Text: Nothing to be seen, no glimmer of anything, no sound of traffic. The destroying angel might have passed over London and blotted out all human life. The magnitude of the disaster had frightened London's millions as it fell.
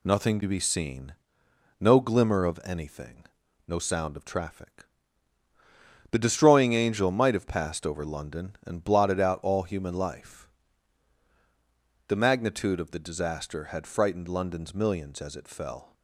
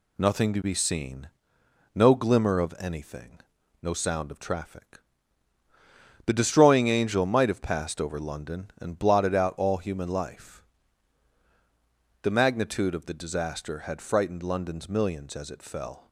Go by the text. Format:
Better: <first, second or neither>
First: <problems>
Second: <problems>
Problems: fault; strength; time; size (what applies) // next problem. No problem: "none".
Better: neither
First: none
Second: none